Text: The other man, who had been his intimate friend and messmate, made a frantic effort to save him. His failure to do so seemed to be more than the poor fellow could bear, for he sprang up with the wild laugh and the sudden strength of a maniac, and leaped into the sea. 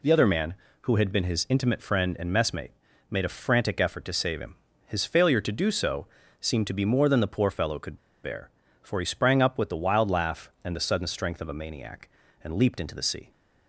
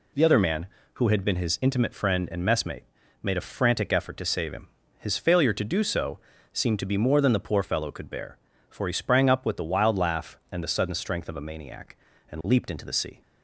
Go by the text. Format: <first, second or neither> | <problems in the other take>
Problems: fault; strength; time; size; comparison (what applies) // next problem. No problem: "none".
second | pauses between "so" and "seemed"; slight; at 6.0 s; 0.34 s long; slight in the second // pauses between "could" and "bear"; slight; at 7.9 s; 0.25 s long